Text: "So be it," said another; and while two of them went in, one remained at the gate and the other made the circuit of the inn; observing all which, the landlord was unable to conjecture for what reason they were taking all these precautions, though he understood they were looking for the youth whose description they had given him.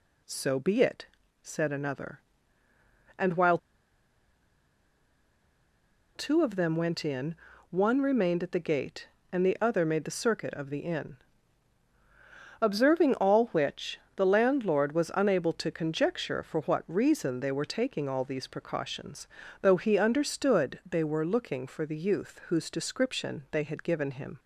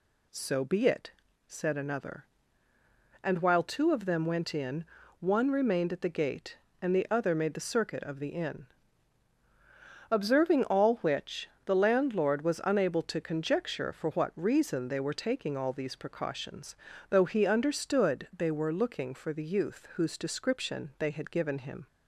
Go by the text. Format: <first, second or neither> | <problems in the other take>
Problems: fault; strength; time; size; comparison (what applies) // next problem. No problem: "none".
second | pauses between "while" and "two"; strong; at 3.5 s; 2.5 s long